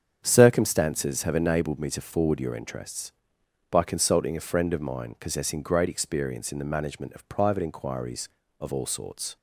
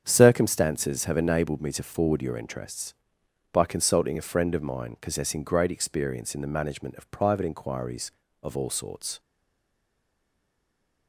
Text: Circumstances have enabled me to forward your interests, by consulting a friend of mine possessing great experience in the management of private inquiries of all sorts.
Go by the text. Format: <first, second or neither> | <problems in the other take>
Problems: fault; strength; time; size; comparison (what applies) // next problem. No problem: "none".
first | starts louder than the rest; strong; until 1.0 s; 8 dB; strong in the first // stays silent after the last word; noticeable; from 9.1 s on; 1.9 s long